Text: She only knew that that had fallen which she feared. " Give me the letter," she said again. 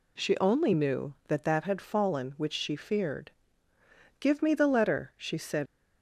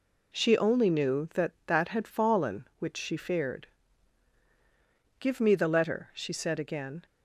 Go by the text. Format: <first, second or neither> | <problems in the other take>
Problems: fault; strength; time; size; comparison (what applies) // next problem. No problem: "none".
second | stops before "again"; at 5.6 s